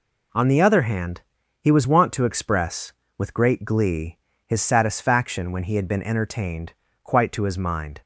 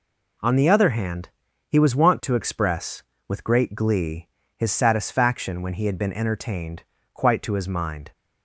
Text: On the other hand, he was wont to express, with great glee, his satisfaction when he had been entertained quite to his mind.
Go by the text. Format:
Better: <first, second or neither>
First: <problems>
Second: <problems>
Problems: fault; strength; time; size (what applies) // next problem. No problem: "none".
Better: neither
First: pauses between "entertained" and "quite"; slight; at 6.7 s; 0.30 s long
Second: pauses between "entertained" and "quite"; slight; at 6.8 s; 0.30 s long